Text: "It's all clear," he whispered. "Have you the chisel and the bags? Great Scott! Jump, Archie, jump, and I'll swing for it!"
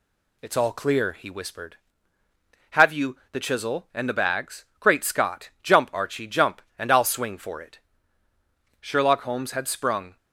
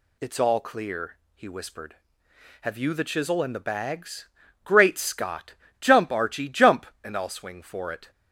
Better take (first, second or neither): second